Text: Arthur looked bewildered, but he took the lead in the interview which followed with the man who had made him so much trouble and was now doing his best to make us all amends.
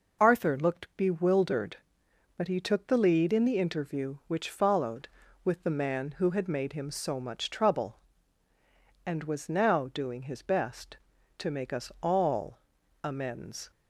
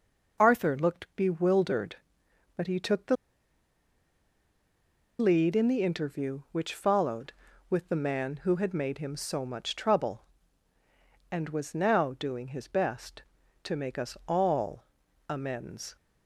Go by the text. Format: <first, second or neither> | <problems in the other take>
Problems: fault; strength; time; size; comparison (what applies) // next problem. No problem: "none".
first | pauses between "the" and "lead"; strong; at 3.1 s; 2.0 s long // pauses between "all" and "amends"; noticeable; at 14.8 s; 0.46 s long; noticeable in the first